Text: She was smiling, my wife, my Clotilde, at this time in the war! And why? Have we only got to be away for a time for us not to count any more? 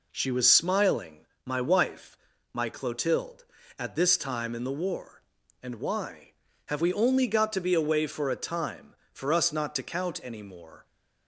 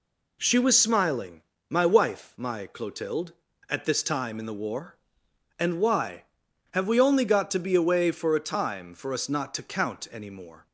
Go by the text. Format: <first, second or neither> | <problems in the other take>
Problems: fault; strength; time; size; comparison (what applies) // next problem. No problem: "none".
neither | none